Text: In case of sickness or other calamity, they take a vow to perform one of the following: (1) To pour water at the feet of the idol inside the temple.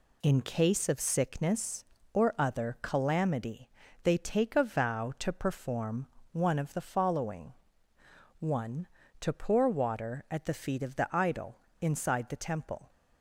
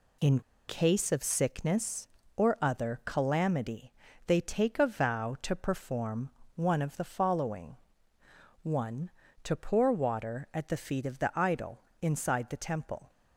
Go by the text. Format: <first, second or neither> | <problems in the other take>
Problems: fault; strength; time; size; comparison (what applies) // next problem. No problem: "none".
first | pauses between "In" and "case"; slight; at 0.4 s; 0.27 s long // pauses between "perform" and "one"; slight; at 6.3 s; 0.24 s long; slight in the first // pauses between "idol" and "inside"; slight; at 11.7 s; 0.22 s long; slight in the first